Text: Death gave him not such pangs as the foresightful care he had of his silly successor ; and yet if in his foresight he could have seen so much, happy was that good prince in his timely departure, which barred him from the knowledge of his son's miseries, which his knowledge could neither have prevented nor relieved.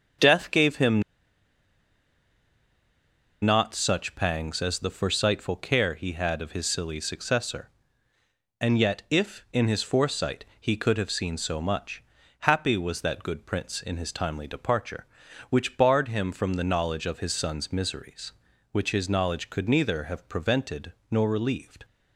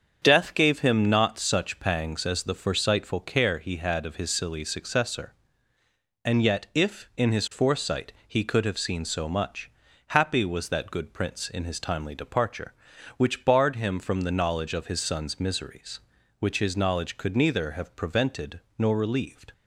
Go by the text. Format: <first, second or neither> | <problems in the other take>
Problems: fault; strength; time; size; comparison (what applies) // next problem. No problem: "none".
second | starts louder than the rest; strong; until 3.6 s; 7.5 dB; strong in the second // pauses between "him" and "not"; strong; at 1.0 s; 2.4 s long // pauses between "prevented" and "nor"; slight; at 20.9 s; 0.20 s long; slight in the second